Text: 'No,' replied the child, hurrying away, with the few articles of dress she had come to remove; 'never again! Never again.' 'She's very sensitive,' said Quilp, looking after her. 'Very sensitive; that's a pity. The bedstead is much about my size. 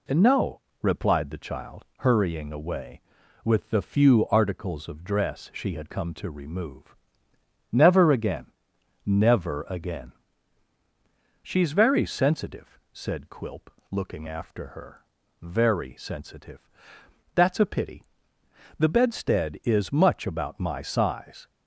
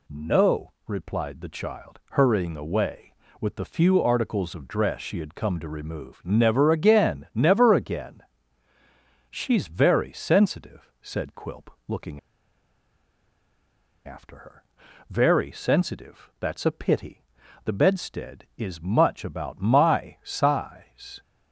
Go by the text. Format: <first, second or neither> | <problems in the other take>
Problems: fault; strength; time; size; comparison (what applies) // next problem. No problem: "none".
first | pauses between "looking" and "after"; strong; at 12.1 s; 1.8 s long